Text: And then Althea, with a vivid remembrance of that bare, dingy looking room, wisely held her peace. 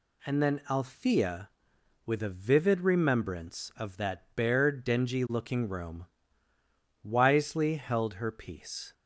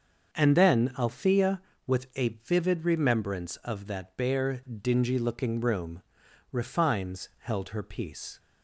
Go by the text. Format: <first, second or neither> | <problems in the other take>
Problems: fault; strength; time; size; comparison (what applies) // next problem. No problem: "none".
first | starts louder than the rest; until 1.3 s; 6.5 dB // pauses between "a" and "vivid"; slight; at 2.2 s; 0.16 s long // says "refines" for "wisely"; at 6.5 s